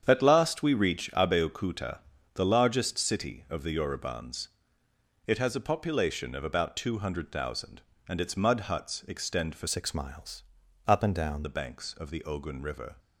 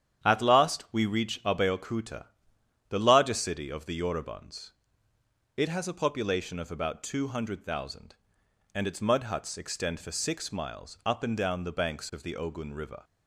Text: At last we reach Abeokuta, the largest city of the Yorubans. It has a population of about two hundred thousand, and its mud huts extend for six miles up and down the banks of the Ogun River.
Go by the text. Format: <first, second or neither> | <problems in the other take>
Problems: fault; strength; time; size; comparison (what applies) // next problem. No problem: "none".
second | starts louder than the rest; strong; until 1.0 s; 8 dB; strong in the second // changes voice from "six" to "down"; from 9.6 to 11.4 s; 1.8 s long // pauses between "miles" and "up"; at 10.4 s; 0.44 s long